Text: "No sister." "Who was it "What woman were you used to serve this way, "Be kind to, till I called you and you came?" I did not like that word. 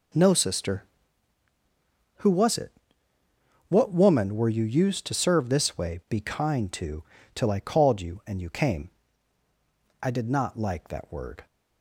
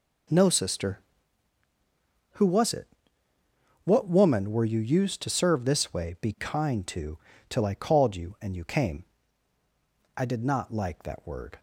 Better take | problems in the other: neither | pauses between "it" and "What"; noticeable; the same in both

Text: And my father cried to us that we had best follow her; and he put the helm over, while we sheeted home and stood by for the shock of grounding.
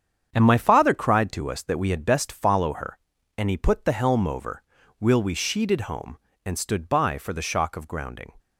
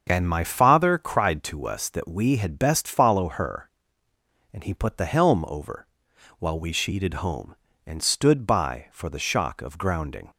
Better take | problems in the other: second | starts louder than the rest; strong; until 1.3 s; 8 dB; also in the second // says "will" for "while"; at 5.0 s

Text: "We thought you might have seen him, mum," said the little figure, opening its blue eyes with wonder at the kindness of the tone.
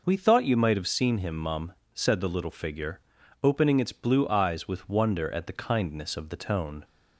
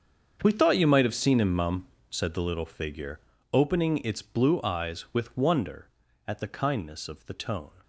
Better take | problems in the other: first | gets quieter; strong; throughout; 16 dB

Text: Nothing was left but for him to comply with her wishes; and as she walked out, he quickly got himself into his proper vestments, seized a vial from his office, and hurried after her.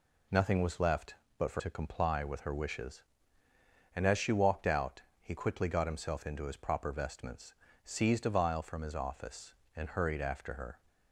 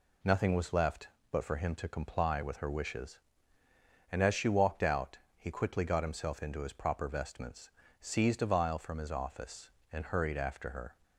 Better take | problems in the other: second | skips "him"; at 1.5 s

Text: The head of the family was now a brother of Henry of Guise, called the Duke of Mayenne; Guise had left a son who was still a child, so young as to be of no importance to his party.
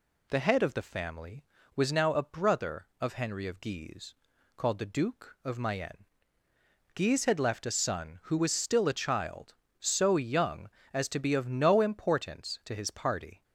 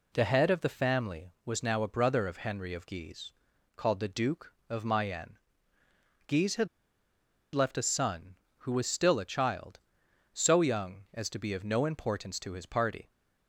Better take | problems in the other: first | pauses between "had" and "left"; noticeable; at 6.6 s; 0.86 s long

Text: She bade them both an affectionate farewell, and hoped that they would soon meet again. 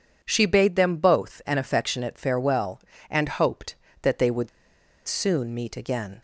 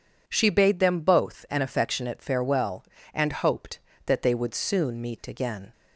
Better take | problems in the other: second | pauses between "would" and "soon"; noticeable; at 4.4 s; 0.59 s long

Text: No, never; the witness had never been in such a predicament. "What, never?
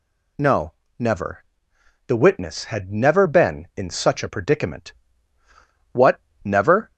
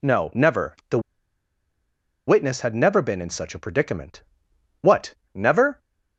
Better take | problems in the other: first | pauses between "the" and "witness"; strong; at 0.9 s; 1.2 s long

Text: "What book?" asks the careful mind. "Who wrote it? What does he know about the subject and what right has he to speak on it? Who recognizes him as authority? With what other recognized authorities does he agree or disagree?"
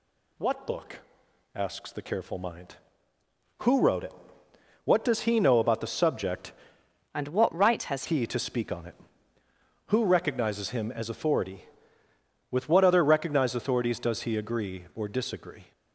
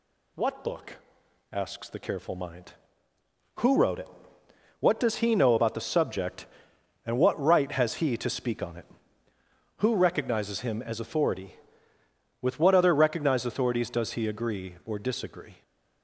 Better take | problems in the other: second | changes voice from "and" to "has"; from 7.1 to 8.0 s; 0.9 s long

